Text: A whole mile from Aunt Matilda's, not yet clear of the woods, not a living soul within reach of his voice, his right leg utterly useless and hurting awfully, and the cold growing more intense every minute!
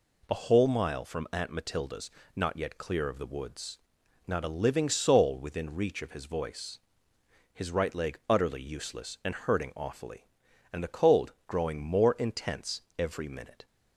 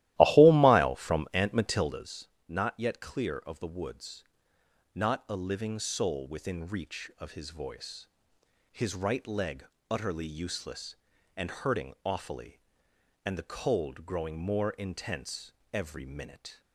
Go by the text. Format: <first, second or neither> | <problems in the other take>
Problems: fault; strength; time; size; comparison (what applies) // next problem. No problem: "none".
first | starts louder than the rest; strong; until 2.0 s; 15 dB // pauses between "leg" and "utterly"; slight; at 9.6 s; 0.24 s long // pauses between "intense" and "every"; slight; at 15.5 s; 0.20 s long; slight in the first